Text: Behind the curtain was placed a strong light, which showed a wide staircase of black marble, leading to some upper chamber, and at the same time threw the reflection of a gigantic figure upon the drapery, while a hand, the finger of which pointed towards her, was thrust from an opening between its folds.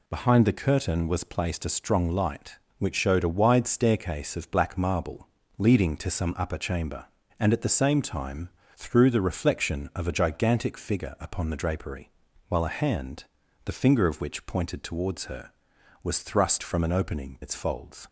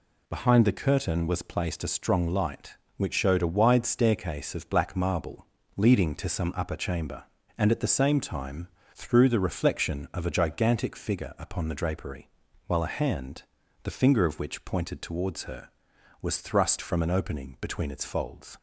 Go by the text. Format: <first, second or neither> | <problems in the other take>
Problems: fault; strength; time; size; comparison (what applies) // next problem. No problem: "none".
second | pauses between "time" and "threw"; slight; at 8.4 s; 0.26 s long; slight in the second // skips "between"; at 17.4 s